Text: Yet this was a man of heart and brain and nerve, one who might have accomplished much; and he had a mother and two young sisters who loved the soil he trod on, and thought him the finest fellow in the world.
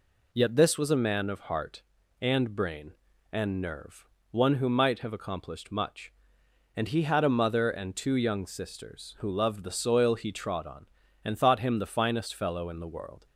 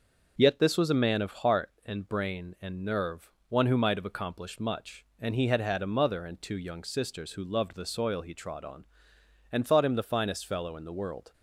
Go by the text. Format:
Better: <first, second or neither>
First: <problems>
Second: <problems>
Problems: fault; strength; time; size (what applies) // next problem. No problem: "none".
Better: first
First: none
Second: starts louder than the rest; noticeable; until 1.3 s; 6 dB // says "had" twice; at 5.6 s